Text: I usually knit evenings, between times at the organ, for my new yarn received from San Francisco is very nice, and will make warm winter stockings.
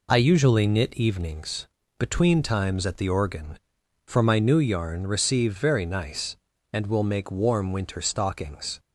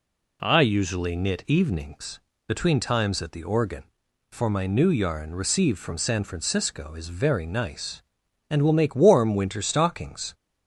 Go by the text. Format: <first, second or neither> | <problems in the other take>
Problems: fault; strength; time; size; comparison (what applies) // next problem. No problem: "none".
second | skips "from San Francisco is"; at 5.5 s